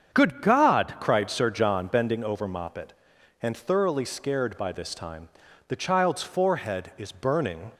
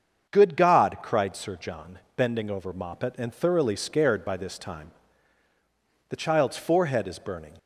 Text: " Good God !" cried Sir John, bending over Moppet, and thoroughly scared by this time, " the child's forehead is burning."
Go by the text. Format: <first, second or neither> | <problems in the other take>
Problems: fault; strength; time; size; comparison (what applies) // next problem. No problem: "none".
neither | starts louder than the rest; strong; the same in both